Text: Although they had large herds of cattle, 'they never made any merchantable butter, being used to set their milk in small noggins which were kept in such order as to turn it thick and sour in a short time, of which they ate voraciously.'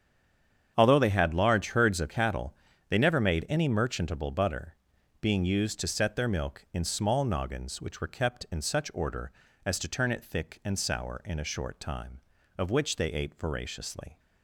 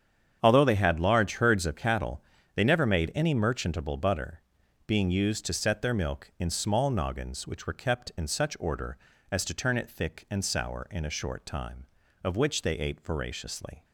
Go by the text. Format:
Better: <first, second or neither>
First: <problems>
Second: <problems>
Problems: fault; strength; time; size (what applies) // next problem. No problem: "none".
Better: second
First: stays silent before the first word; slight; until 0.7 s; 0.7 s long // starts louder than the rest; strong; until 1.7 s; 8 dB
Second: starts louder than the rest; strong; until 1.4 s; 8 dB